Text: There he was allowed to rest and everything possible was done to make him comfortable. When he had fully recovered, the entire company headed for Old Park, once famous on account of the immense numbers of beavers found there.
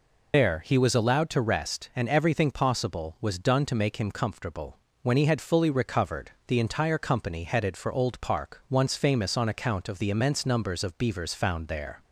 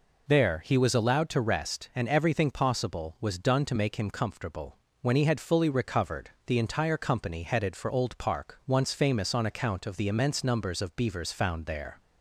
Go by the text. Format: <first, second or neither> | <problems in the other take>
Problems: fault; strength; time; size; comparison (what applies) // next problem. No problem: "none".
second | loses the start of "There"; at 0.3 s; 55 ms